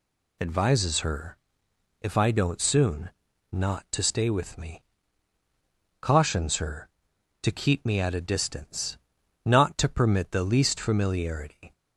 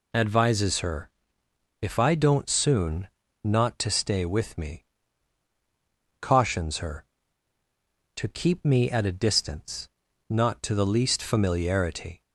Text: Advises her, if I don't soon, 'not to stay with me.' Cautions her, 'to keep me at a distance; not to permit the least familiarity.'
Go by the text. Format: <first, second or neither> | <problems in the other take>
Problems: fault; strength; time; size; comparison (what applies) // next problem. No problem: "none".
first | skips "permit"; at 10.7 s